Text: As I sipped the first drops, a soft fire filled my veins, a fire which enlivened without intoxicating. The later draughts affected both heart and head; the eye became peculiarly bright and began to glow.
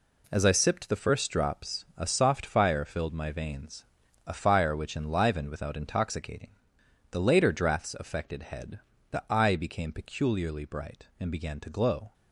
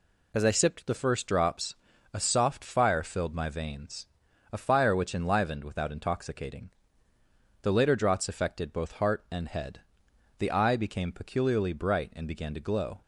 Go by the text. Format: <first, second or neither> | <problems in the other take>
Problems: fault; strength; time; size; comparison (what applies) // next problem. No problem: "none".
second | skips "both heart and"; at 8.4 s